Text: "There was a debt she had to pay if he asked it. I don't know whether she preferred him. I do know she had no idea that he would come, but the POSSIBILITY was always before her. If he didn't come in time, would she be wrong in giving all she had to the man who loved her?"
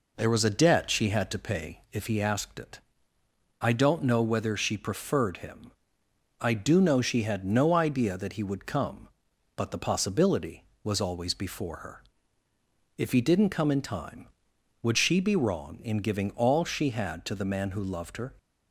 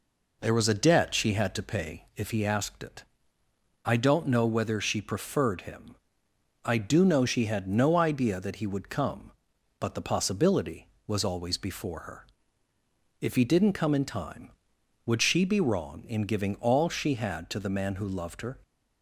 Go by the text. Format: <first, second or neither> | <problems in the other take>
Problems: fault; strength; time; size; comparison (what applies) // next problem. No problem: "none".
neither | none